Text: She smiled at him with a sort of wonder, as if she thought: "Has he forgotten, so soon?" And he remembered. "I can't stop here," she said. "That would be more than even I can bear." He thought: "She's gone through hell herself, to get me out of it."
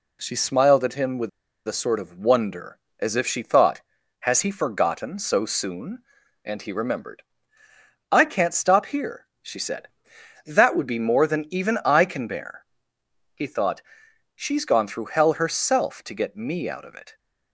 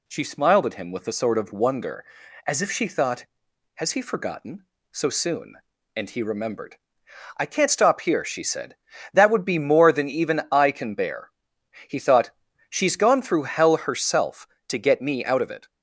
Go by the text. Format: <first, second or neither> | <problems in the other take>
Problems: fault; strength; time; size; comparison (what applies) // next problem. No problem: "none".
second | pauses between "with" and "a"; at 1.2 s; 0.38 s long